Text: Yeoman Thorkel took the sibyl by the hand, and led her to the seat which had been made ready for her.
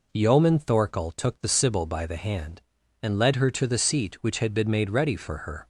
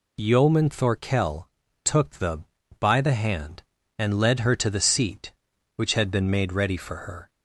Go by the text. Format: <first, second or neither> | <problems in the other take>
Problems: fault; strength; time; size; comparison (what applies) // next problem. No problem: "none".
first | pauses between "Thorkel" and "took"; slight; at 1.4 s; 0.36 s long // skips "sibyl"; at 2.6 s